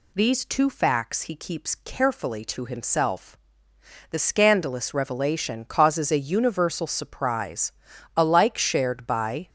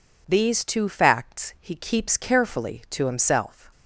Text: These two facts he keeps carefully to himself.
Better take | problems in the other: second | goes on to say "The scandalous revelation causes a universal surprise alike shared by"; strong; from 4.1 s on; 5.3 s long

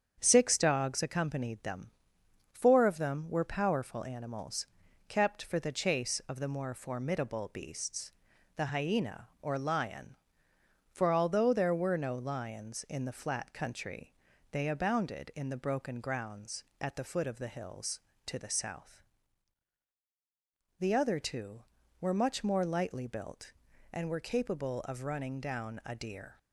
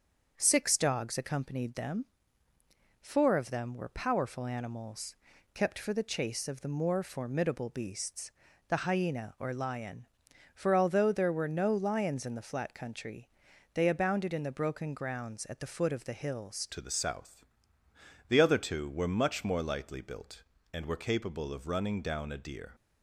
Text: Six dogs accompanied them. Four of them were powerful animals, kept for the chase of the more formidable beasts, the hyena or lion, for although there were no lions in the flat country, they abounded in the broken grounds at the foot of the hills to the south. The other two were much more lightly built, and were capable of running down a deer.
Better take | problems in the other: first | starts louder than the rest; until 1.3 s; 7 dB; strong in the first // changes voice at "to"; from 16.6 s on; 6.1 s long

